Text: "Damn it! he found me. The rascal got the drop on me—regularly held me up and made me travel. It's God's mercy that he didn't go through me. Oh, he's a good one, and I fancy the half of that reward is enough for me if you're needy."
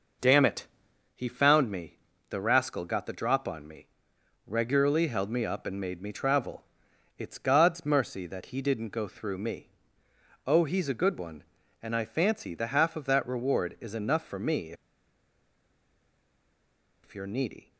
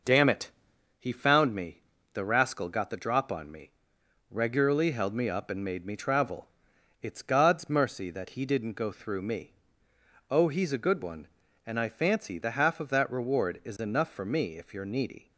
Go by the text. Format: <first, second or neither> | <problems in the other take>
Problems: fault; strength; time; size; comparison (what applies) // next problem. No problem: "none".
second | pauses between "me" and "if"; strong; at 14.7 s; 2.3 s long